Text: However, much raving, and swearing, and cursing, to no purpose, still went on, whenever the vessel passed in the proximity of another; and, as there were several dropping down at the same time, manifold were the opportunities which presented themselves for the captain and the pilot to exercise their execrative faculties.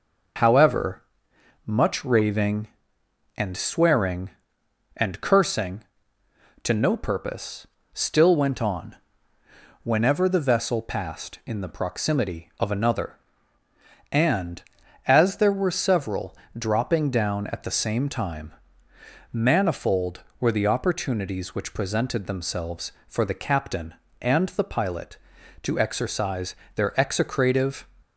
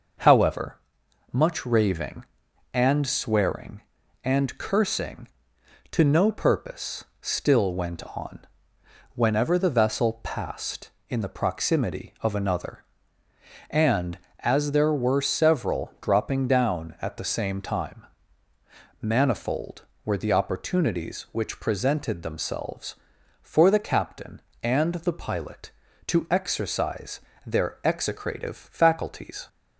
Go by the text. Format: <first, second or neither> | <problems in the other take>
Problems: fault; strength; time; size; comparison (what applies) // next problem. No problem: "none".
second | pauses between "several" and "dropping"; slight; at 16.3 s; 0.22 s long // pauses between "exercise" and "their"; slight; at 26.5 s; 0.20 s long; slight in the second // stops before "faculties"; at 28.0 s